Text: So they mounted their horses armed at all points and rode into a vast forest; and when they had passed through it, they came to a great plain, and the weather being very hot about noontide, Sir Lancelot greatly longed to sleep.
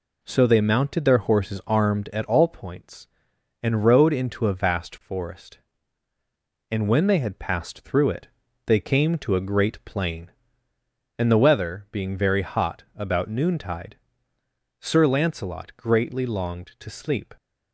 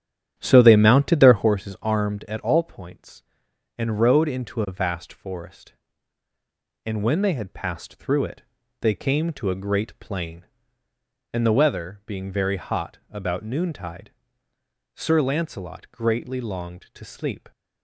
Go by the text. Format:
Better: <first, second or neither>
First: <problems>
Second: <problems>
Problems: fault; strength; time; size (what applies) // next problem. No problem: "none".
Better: first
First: none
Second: starts louder than the rest; strong; until 1.6 s; 10 dB